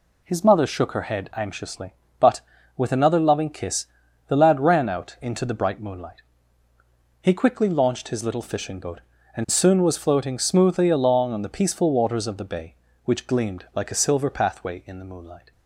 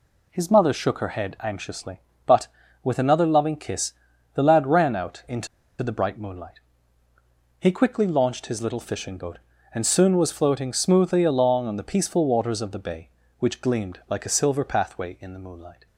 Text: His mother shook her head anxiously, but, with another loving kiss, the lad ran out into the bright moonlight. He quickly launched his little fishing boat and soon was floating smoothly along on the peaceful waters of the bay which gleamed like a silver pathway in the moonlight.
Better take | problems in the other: first | pauses between "into" and "the"; slight; at 5.4 s; 0.34 s long

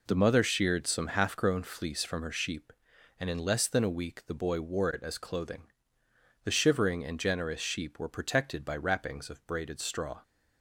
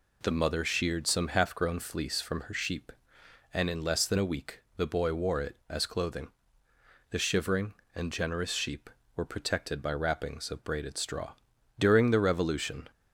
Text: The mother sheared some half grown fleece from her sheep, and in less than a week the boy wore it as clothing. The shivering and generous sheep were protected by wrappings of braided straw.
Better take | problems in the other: first | pauses between "week" and "the"; slight; at 4.6 s; 0.16 s long // goes on to say "During the Revolution"; noticeable; from 11.7 s on; 1.1 s long

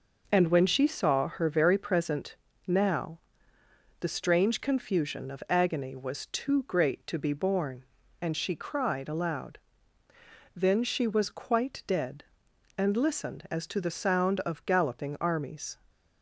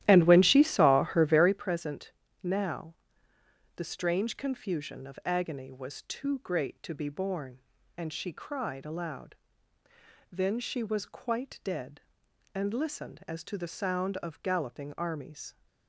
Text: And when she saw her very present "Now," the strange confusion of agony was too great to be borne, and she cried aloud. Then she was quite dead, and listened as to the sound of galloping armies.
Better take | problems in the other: first | starts louder than the rest; strong; until 1.7 s; 13.5 dB // pauses between "present" and "Now"; slight; at 2.0 s; 0.32 s long; slight in the first

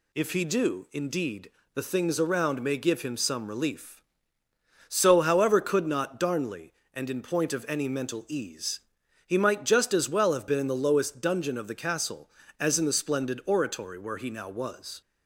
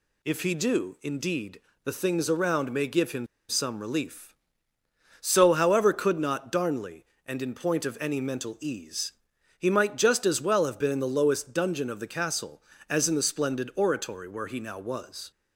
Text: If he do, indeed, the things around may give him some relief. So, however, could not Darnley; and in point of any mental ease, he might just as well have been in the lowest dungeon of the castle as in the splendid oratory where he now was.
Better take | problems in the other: first | pauses between "him" and "some"; slight; at 3.2 s; 0.22 s long

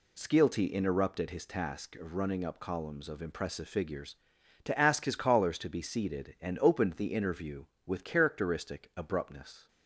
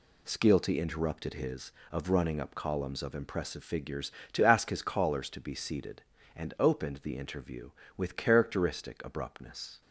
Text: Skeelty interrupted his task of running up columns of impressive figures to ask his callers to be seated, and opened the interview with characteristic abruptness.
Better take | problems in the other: first | skips "task"; at 1.8 s

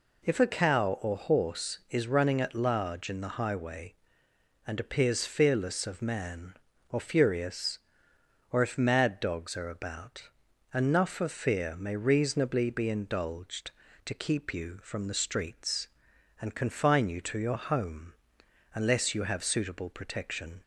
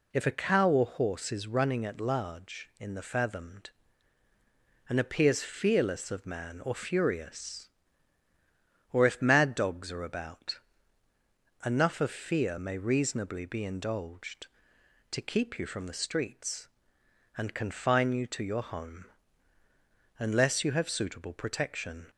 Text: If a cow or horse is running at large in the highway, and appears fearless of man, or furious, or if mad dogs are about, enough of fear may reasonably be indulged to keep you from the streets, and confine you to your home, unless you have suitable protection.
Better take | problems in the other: first | says "fathomed" for "highway"; at 3.0 s

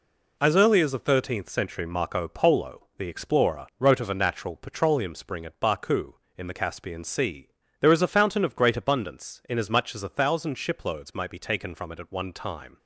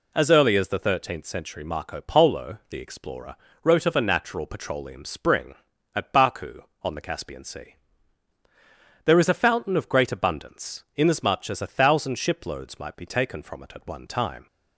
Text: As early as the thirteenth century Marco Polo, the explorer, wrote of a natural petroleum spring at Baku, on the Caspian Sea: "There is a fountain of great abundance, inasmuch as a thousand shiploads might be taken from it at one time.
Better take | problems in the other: second | says "in" for "on"; at 6.3 s

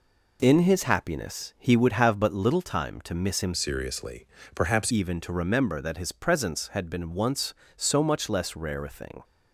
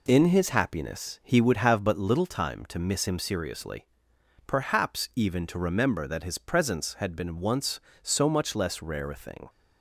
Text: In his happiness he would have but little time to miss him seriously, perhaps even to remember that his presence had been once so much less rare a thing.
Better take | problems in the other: second | changes voice from "seriously" to "perhaps"; from 3.5 to 4.9 s; 1.4 s long

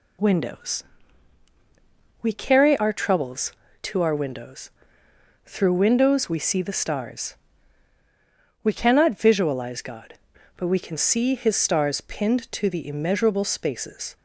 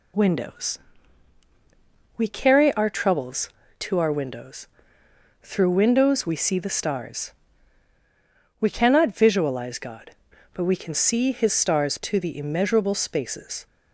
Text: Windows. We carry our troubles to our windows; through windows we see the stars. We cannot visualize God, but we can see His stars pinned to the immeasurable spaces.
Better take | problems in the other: first | skips "pinned"; at 11.9 s

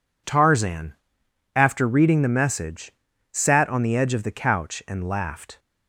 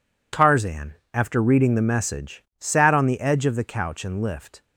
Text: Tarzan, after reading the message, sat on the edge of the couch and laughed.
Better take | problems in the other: first | says "lift" for "laughed"; at 4.1 s

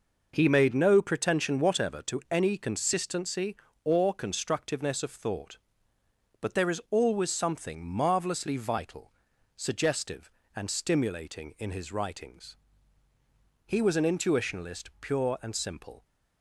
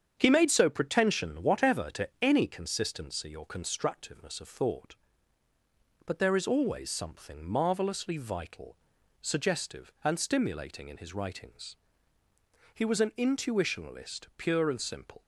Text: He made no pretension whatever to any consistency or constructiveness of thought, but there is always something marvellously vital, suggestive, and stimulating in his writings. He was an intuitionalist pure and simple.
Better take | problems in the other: first | starts louder than the rest; strong; until 1.1 s; 8 dB // says "so" for "no"; at 0.4 s

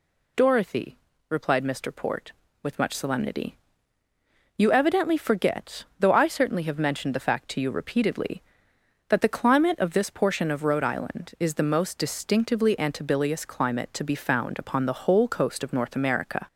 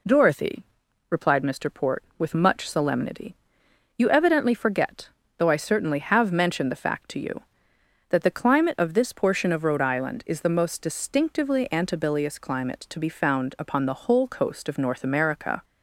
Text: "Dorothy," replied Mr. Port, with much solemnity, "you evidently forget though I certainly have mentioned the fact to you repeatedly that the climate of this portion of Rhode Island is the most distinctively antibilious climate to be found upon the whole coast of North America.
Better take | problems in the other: first | pauses between "forget" and "though"; slight; at 5.0 s; 0.28 s long; slight in the first // skips "repeatedly"; at 7.7 s

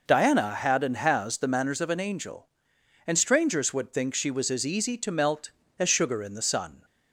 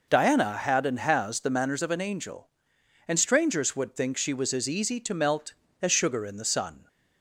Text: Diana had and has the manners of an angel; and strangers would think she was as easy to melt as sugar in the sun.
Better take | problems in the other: neither | none

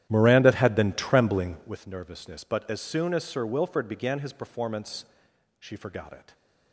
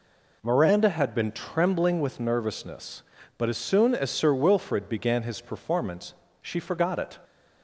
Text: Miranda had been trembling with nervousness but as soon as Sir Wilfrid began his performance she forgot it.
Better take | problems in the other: second | starts louder than the rest; strong; until 1.8 s; 11.5 dB // pauses between "performance" and "she"; noticeable; at 5.0 s; 0.54 s long; slight in the second

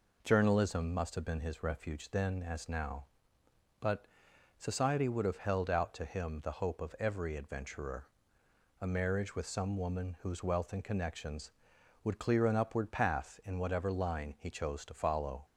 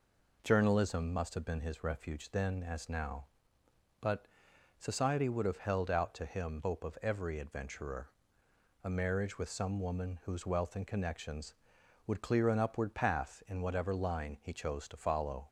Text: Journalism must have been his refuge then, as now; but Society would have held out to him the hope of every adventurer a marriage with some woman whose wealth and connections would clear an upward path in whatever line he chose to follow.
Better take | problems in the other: first | pauses between "but" and "Society"; noticeable; at 4.2 s; 0.52 s long; noticeable in the first // skips "the"; at 6.6 s // pauses between "adventurer" and "a"; noticeable; at 8.0 s; 0.74 s long; noticeable in the first

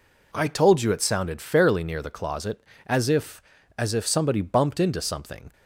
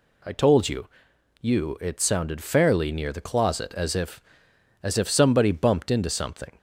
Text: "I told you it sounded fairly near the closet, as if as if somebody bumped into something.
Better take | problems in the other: first | says "you" twice; at 1.4 s

